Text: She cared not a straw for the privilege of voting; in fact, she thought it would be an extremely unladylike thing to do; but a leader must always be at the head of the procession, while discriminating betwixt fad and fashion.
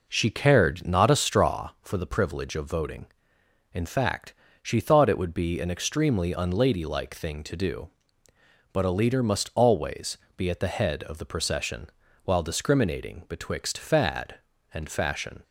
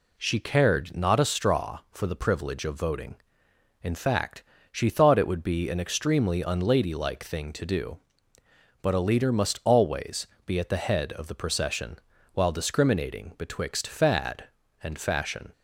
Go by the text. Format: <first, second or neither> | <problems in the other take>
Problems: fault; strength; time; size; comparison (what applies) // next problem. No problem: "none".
second | starts louder than the rest; noticeable; until 1.8 s; 4.5 dB // pauses between "always" and "be"; slight; at 10.1 s; 0.18 s long; slight in the second